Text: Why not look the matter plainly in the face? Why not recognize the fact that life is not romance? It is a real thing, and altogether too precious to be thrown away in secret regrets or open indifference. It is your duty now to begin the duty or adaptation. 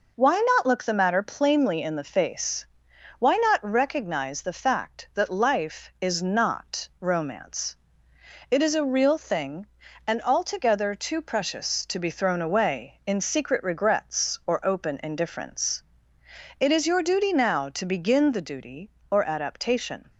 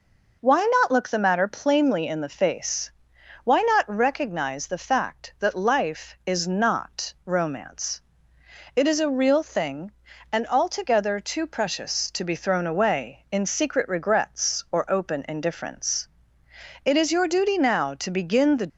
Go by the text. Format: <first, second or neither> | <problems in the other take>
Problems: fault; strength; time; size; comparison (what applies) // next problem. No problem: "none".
first | stops before "duty or adaptation"; at 18.6 s